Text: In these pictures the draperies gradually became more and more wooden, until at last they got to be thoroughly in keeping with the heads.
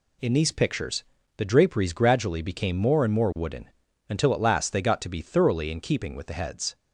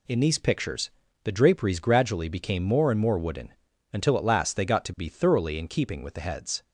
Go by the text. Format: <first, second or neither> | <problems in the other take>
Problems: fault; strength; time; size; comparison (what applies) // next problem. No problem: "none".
neither | pauses between "pictures" and "the"; slight; the same in both